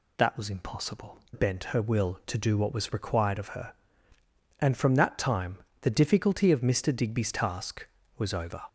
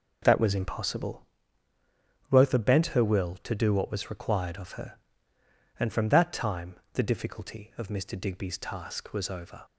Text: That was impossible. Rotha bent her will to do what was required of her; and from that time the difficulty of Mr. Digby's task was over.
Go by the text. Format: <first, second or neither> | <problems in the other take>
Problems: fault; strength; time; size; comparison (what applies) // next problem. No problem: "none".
second | skips "Rotha"; at 1.2 s // pauses between "time" and "the"; slight; at 5.5 s; 0.24 s long; slight in the second